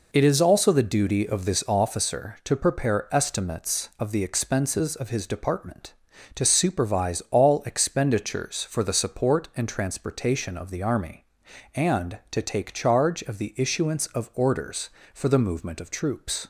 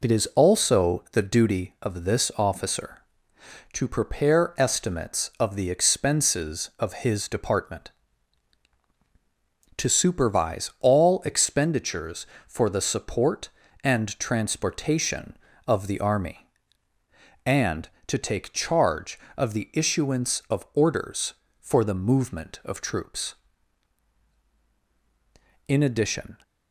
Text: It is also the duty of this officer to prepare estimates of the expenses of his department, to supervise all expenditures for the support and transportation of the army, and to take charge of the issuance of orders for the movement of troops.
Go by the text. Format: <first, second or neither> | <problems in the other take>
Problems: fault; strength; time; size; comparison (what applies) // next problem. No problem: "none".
first | goes on to say "In addition"; noticeable; from 25.6 s on; 0.74 s long